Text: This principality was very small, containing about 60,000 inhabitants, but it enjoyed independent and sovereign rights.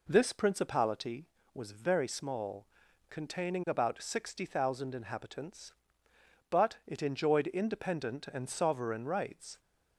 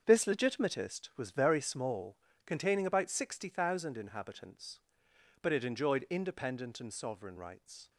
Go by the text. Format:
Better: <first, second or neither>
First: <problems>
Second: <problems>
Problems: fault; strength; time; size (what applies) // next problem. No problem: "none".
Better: first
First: none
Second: starts louder than the rest; until 1.0 s; 7 dB // says "legitimatist" for "principality"; at 0.2 s